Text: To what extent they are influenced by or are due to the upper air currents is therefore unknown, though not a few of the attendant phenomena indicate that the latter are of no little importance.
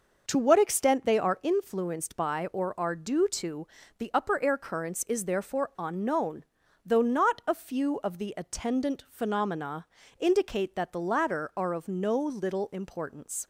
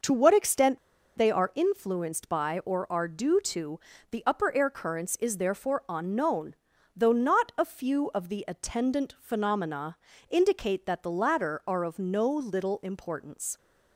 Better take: first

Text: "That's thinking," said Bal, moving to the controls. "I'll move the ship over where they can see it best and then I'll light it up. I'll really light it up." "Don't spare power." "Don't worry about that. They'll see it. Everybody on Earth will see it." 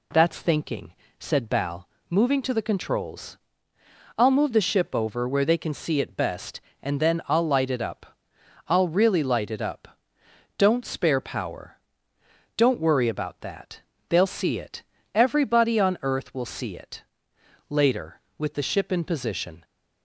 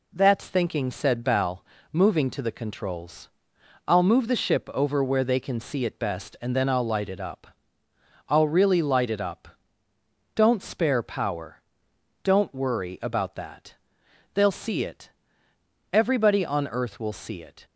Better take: second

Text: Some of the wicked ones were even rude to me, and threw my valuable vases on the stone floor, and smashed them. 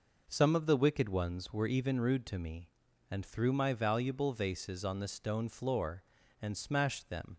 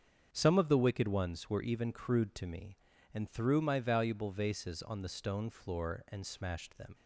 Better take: first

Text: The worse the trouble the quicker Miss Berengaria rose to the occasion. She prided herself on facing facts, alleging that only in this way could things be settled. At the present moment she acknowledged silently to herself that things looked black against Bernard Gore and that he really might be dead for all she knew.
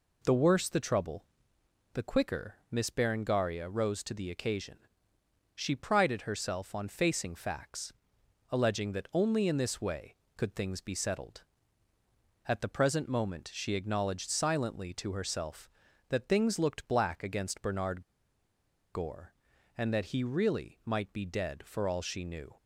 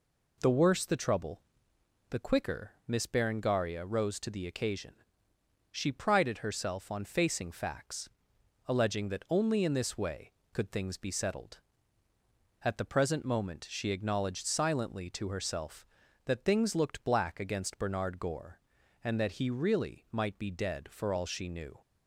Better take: second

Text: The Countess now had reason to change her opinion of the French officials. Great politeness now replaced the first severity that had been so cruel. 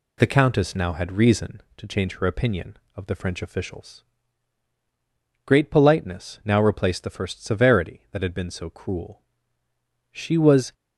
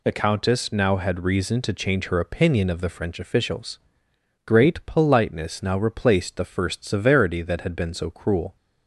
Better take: second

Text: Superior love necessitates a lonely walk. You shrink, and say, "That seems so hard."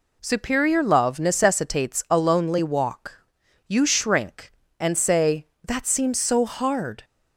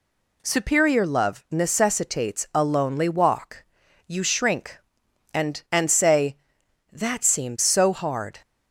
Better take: first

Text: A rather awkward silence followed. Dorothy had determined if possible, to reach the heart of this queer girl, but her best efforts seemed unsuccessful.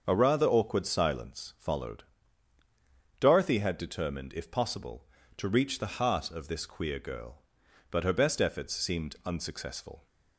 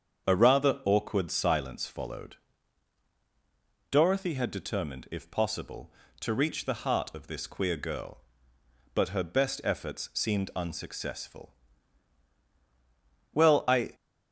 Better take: first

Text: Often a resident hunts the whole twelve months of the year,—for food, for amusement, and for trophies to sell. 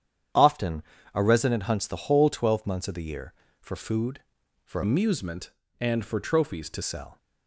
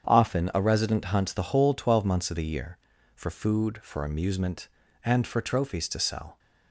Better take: second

